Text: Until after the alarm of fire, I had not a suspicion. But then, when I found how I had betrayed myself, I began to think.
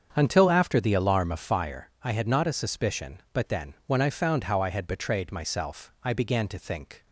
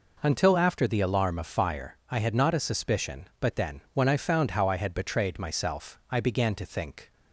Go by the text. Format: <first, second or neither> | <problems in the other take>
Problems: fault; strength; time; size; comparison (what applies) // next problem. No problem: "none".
second | starts louder than the rest; strong; until 1.5 s; 7 dB